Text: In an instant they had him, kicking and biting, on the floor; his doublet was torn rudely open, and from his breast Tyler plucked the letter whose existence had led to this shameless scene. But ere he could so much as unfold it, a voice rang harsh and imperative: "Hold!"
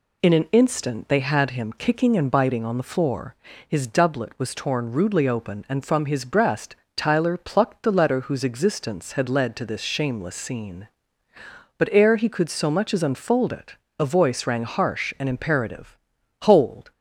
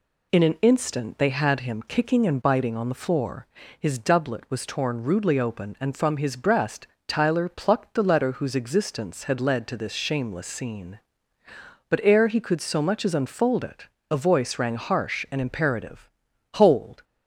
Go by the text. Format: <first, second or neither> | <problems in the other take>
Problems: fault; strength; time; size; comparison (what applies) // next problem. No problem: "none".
neither | pauses between "breast" and "Tyler"; slight; the same in both